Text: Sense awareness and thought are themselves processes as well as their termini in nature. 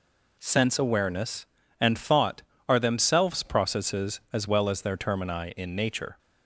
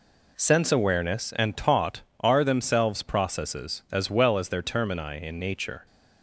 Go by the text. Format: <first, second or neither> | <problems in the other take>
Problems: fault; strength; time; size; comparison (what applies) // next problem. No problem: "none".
first | says "taught" for "thought"; at 1.5 s